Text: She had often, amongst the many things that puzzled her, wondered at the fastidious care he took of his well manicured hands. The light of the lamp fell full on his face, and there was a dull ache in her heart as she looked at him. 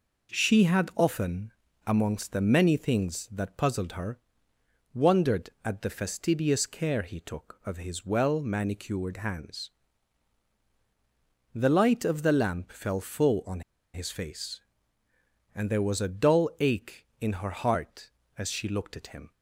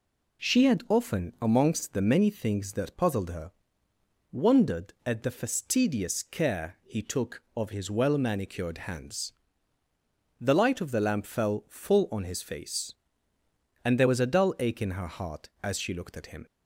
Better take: second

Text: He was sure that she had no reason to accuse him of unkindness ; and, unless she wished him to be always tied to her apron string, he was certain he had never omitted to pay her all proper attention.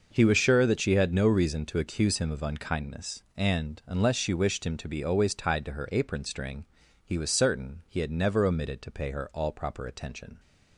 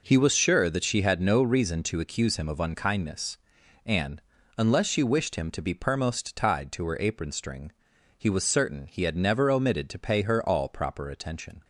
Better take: first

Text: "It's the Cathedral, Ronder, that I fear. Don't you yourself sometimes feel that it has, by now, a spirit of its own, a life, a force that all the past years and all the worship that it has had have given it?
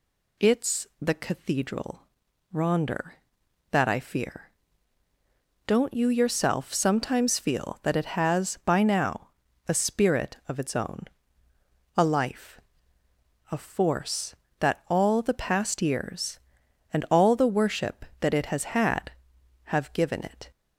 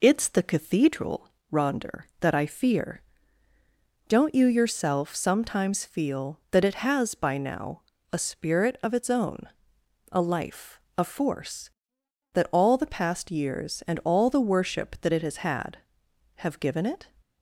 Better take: first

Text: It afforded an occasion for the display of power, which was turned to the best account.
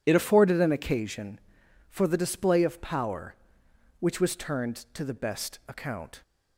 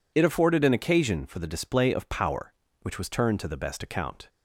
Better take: second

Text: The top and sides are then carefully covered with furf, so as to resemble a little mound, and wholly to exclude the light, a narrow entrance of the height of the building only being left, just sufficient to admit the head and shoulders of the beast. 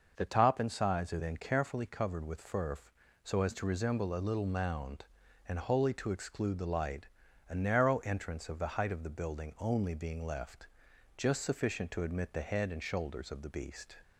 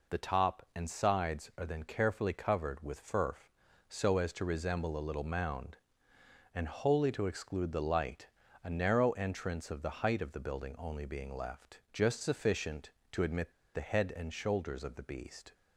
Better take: first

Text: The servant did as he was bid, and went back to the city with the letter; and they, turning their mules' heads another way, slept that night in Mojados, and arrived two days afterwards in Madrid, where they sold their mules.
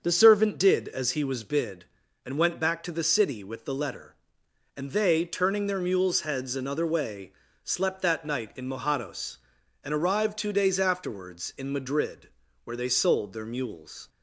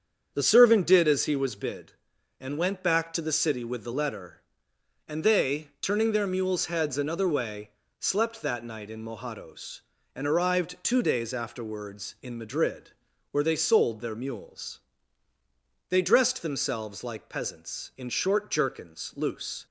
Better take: first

